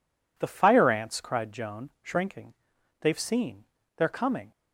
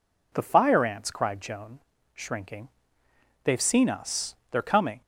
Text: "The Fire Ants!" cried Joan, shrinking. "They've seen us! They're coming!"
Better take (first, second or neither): second